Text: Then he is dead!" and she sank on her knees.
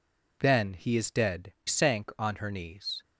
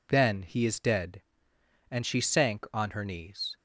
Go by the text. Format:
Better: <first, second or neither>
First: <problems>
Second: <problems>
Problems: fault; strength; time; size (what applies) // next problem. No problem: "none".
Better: second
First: skips "and she"; at 1.5 s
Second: none